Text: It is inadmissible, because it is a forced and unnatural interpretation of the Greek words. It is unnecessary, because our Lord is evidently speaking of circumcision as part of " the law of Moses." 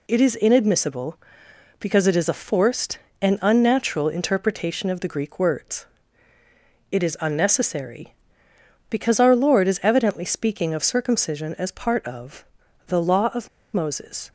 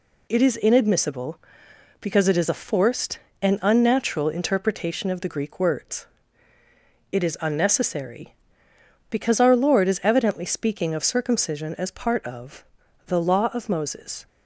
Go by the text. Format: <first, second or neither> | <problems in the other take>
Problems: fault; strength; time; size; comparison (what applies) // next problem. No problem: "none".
second | pauses between "of" and "Moses"; slight; at 13.4 s; 0.24 s long